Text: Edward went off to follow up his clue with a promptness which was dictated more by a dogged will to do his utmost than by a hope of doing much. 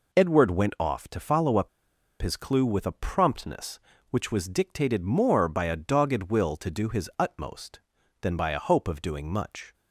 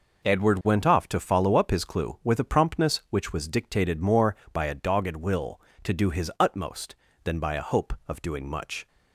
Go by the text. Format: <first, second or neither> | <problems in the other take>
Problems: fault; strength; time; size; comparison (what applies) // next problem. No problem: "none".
second | pauses between "up" and "his"; noticeable; at 1.6 s; 0.54 s long